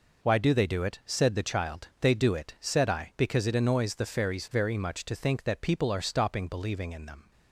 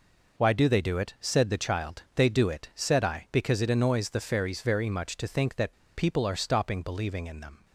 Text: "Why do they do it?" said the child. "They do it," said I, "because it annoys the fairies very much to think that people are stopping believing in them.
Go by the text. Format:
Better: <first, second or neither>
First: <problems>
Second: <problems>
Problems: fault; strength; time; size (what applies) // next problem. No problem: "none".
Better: first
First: none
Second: pauses between "that" and "people"; slight; at 5.7 s; 0.23 s long